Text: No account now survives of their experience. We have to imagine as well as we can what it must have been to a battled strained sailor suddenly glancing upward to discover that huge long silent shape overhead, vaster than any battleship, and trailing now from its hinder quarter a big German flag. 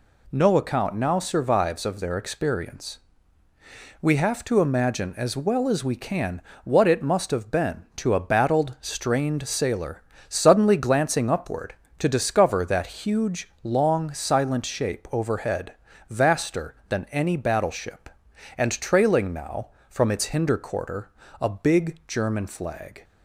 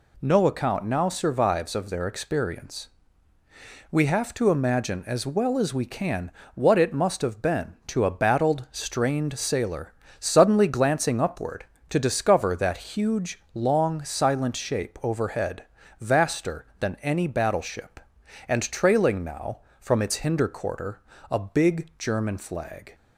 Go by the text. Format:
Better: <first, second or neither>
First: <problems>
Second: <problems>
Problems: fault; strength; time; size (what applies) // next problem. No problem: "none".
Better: neither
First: pauses between "can" and "what"; slight; at 6.4 s; 0.22 s long // pauses between "sailor" and "suddenly"; slight; at 10.0 s; 0.26 s long // pauses between "quarter" and "a"; slight; at 21.0 s; 0.32 s long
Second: pauses between "can" and "what"; slight; at 6.3 s; 0.22 s long // pauses between "sailor" and "suddenly"; slight; at 9.9 s; 0.26 s long // pauses between "quarter" and "a"; slight; at 20.9 s; 0.31 s long